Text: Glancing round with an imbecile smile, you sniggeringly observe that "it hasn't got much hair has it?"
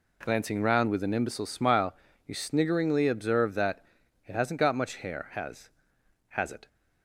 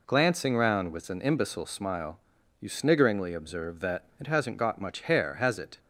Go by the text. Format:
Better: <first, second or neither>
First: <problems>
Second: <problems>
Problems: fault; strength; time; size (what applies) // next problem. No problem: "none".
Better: second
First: pauses between "that" and "it"; at 3.8 s; 0.44 s long // says "has" twice; at 6.3 s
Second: pauses between "that" and "it"; slight; at 4.0 s; 0.16 s long